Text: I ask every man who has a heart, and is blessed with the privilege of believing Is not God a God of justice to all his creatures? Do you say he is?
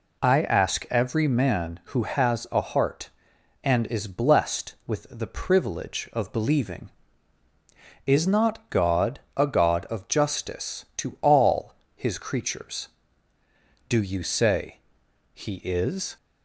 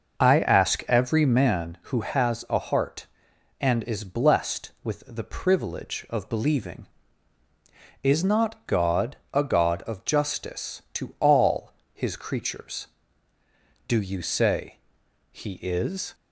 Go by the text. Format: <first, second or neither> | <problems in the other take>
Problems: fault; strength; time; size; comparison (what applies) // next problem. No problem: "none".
first | starts louder than the rest; noticeable; until 1.7 s; 6 dB // pauses between "God" and "a"; slight; at 9.1 s; 0.16 s long; slight in the first // pauses between "all" and "his"; slight; at 11.7 s; 0.20 s long; slight in the first // pauses between "say" and "he"; noticeable; at 14.7 s; 0.55 s long; noticeable in the first